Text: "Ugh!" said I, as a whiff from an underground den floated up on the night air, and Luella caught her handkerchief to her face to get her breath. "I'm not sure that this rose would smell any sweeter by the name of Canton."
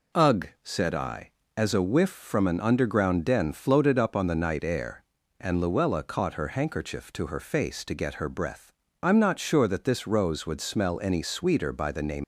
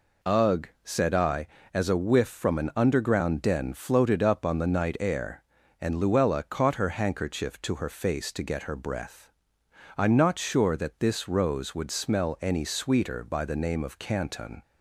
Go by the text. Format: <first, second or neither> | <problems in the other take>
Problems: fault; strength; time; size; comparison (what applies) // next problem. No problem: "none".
second | stops before "of Canton"; at 12.2 s